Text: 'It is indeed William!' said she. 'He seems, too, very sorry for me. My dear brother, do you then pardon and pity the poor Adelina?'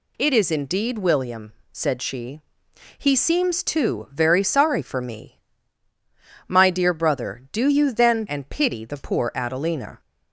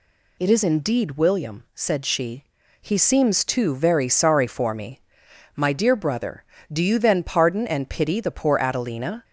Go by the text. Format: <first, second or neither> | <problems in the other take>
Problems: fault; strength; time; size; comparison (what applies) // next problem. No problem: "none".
second | skips "pardon"; at 8.2 s